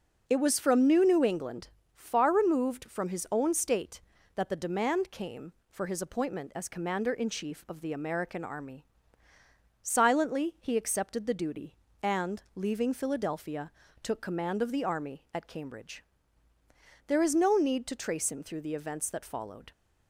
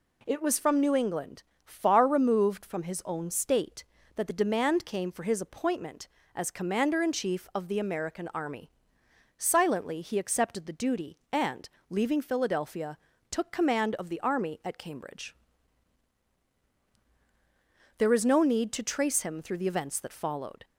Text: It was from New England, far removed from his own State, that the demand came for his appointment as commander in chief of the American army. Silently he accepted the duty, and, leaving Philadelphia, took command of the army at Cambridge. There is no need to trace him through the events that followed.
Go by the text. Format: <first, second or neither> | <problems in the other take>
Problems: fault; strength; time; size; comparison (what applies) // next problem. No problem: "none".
second | says "New" twice; at 1.0 s